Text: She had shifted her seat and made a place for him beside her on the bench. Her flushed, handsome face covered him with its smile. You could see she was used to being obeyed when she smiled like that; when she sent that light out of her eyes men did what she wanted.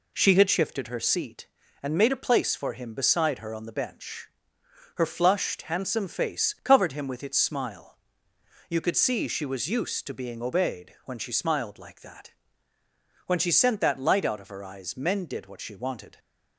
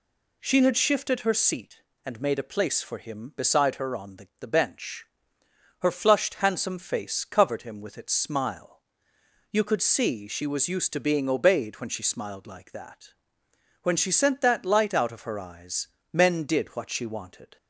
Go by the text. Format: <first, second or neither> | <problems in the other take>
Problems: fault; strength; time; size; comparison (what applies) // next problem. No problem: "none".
first | says "the" twice; at 4.3 s // pauses between "eyes" and "men"; slight; at 15.8 s; 0.22 s long